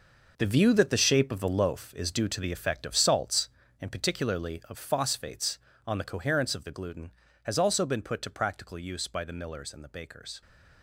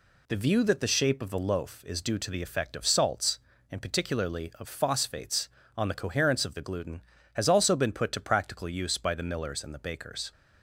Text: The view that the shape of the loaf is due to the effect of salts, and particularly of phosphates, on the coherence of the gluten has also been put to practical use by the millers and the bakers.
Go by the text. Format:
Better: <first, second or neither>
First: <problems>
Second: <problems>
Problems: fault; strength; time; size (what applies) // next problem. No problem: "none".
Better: second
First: gets quieter; strong; throughout; 11.5 dB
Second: none